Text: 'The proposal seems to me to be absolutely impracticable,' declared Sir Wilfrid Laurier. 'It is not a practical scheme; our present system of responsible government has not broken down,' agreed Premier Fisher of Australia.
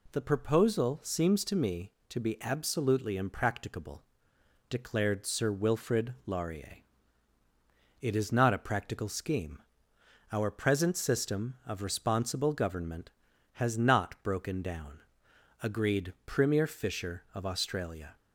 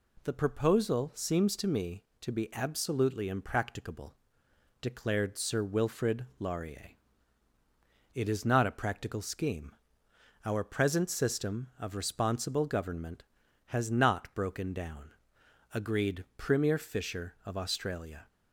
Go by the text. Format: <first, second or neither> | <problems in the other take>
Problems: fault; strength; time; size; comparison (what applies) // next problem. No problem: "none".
neither | none